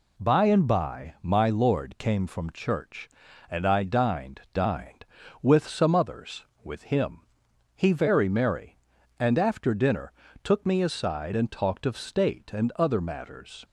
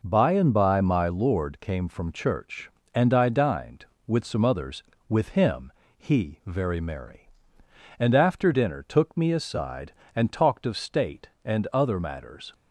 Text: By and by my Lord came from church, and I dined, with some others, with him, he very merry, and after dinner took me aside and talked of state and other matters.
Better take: second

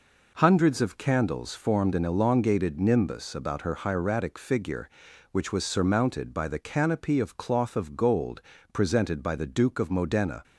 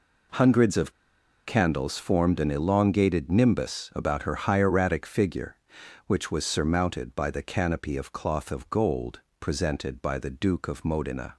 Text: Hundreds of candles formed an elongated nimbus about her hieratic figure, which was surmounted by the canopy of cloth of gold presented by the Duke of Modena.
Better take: first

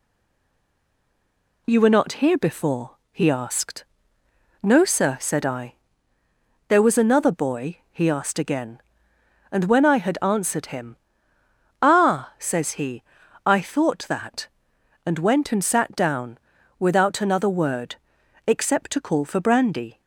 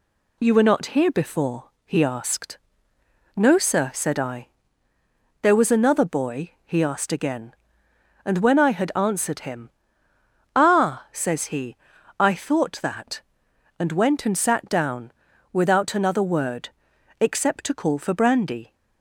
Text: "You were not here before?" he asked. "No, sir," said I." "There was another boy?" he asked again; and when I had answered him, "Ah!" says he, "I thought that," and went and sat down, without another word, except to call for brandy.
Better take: second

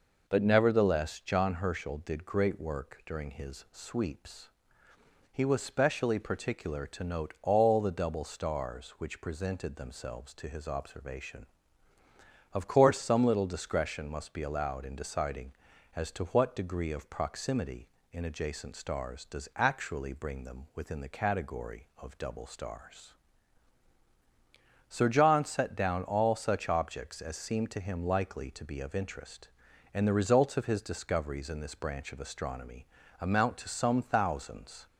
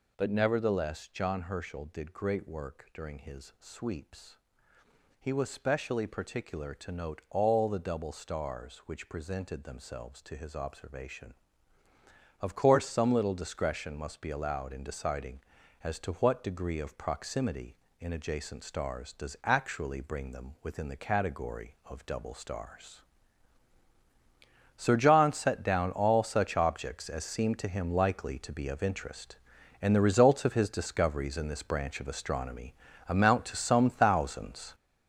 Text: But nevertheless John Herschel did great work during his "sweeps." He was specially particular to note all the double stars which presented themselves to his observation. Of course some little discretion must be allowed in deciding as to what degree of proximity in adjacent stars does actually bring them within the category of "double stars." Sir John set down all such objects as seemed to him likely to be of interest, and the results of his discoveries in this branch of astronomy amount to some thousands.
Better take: first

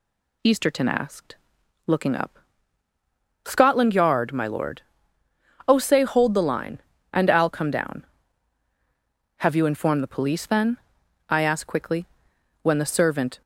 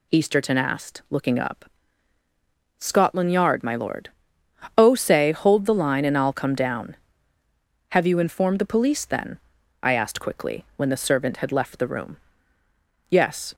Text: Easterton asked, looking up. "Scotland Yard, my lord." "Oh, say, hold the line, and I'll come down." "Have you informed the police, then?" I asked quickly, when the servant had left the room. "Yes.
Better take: second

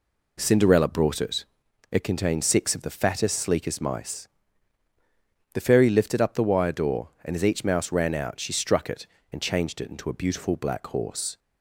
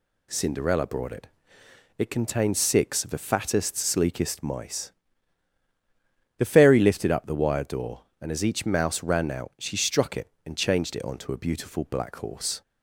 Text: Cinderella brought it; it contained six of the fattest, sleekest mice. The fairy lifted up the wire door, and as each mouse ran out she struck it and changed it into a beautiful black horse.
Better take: first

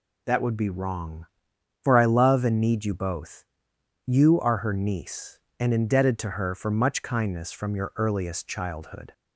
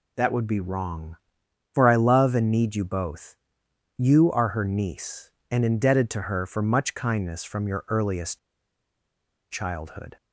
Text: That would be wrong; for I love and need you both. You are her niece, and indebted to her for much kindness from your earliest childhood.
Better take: first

